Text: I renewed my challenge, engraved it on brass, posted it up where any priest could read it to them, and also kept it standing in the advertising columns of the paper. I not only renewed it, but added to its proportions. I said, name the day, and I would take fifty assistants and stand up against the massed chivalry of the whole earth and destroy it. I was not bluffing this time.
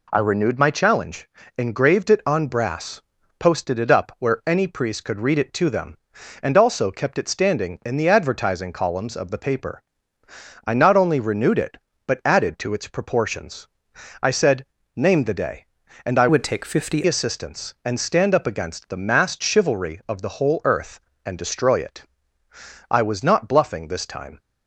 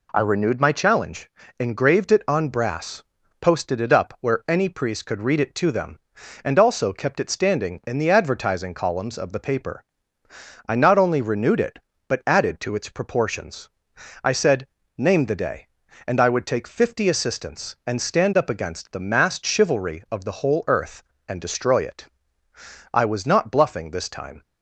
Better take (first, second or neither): second